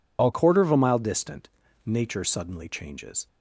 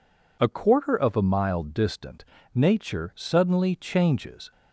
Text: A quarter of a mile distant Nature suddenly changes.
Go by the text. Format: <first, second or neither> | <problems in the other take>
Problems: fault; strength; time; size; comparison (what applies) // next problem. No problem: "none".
second | changes voice at "quarter"; from 0.3 s on; 2.9 s long // pauses between "distant" and "Nature"; at 1.4 s; 0.38 s long; slight in the second